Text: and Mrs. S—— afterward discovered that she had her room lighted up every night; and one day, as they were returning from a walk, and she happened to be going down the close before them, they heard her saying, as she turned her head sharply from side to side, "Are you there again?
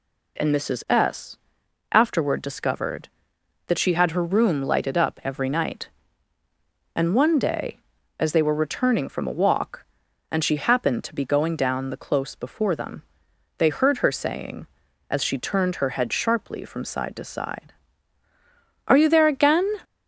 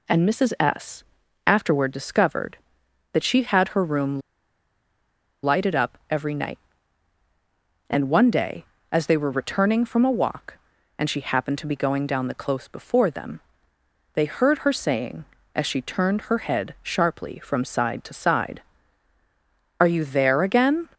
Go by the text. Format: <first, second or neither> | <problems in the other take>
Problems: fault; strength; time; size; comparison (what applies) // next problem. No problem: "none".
first | pauses between "room" and "lighted"; at 4.2 s; 1.2 s long